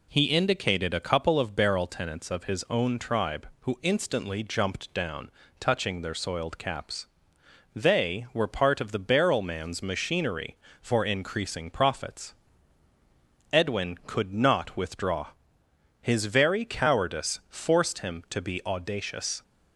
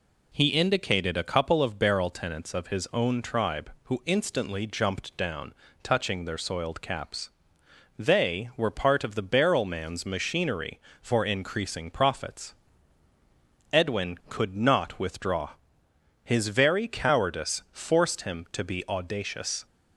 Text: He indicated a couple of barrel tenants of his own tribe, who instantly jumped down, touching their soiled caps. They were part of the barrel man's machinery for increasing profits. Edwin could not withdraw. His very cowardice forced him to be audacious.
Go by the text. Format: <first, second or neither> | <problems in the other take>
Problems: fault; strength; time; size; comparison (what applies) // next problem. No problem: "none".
neither | none